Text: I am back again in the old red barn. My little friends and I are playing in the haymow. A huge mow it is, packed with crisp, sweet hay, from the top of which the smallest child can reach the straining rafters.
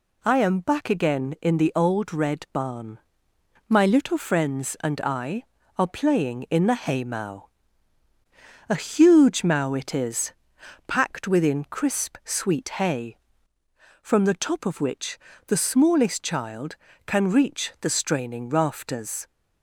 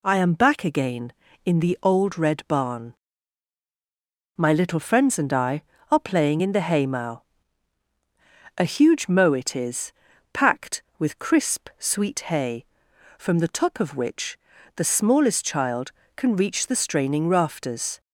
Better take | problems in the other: second | says "within" for "with"; at 11.2 s // pauses between "which" and "the"; slight; at 15.1 s; 0.30 s long; also in the second

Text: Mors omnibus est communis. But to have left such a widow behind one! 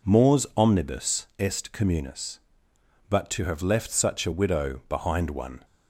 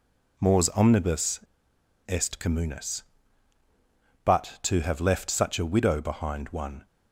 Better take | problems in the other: first | pauses between "omnibus" and "est"; noticeable; at 1.3 s; 0.69 s long

